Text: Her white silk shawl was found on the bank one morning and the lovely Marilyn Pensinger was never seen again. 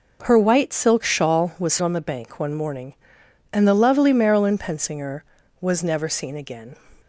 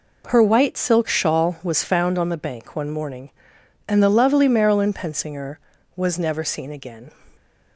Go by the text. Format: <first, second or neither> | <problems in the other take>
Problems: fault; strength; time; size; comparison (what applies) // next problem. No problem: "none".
second | skips "found"; at 1.8 s